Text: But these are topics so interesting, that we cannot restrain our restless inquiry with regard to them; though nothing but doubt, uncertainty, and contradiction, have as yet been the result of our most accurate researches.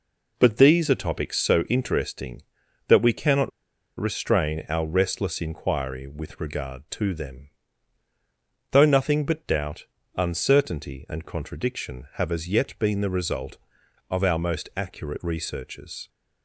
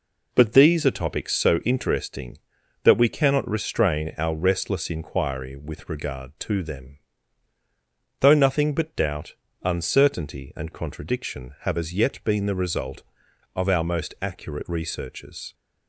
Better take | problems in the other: second | pauses between "cannot" and "restrain"; noticeable; at 3.5 s; 0.49 s long

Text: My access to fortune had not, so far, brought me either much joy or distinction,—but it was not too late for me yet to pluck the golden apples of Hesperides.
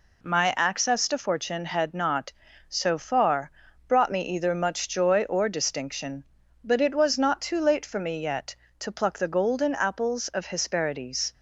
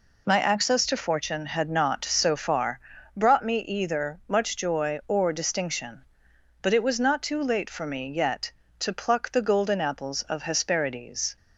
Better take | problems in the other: neither | none

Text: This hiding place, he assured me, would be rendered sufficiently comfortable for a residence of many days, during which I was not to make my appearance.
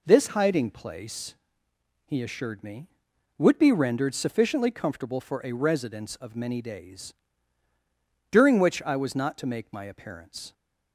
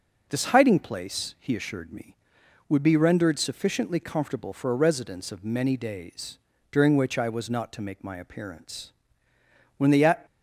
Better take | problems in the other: first | goes on to say "When the"; slight; from 9.7 s on; 0.48 s long

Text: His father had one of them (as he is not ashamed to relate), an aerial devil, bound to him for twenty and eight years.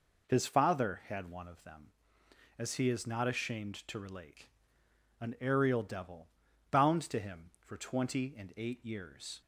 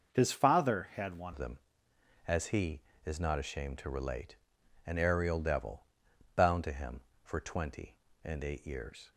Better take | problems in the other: first | changes voice at "of"; from 1.3 s on; 7.8 s long

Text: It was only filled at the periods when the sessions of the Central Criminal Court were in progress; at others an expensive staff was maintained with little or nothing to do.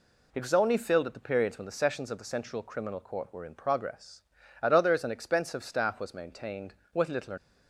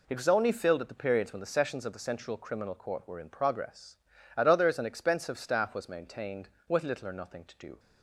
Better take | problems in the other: second | stops before "nothing to do"; at 7.3 s

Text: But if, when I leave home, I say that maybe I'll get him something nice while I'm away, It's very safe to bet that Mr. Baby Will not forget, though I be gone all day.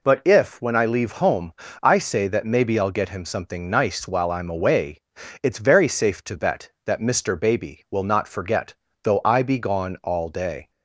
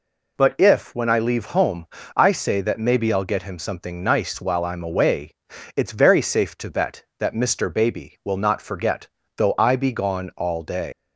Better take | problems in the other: first | leaves "day" unfinished; at 10.9 s; 110 ms

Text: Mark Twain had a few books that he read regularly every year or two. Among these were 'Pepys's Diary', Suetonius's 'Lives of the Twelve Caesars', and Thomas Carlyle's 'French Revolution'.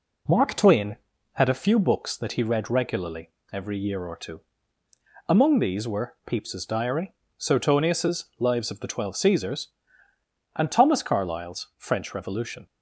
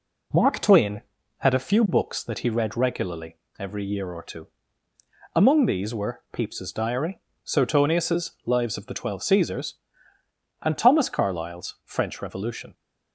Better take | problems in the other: neither | pauses between "regularly" and "every"; slight; the same in both // pauses between "Suetonius's" and "Lives"; slight; the same in both

